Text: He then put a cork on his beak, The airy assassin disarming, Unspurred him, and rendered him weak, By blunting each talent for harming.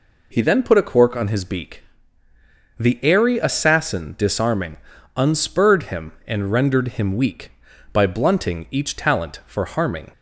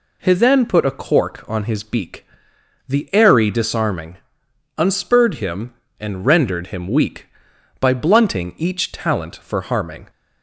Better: first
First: none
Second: skips "assassin"; at 3.4 s

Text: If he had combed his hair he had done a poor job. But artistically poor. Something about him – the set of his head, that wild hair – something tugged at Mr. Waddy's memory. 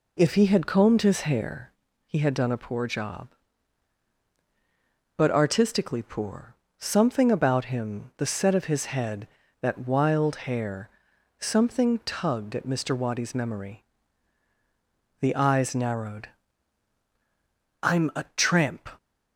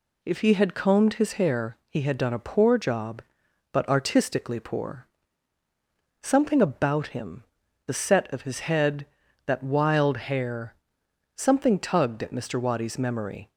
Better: second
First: pauses between "hair" and "he"; at 1.6 s; 0.38 s long // goes on to say "The eyes narrowed I'm a tramp"; strong; from 15.1 s on; 3.6 s long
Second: none

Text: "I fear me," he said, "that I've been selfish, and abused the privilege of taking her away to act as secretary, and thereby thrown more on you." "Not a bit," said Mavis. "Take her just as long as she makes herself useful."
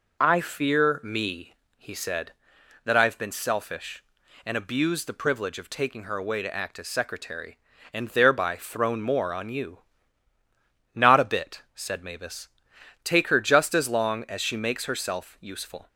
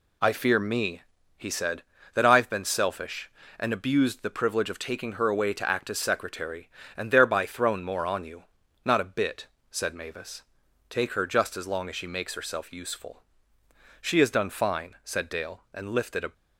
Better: first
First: none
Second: goes on to say "She has done fine said Dale and lifted a"; strong; from 14.0 s on; 2.3 s long

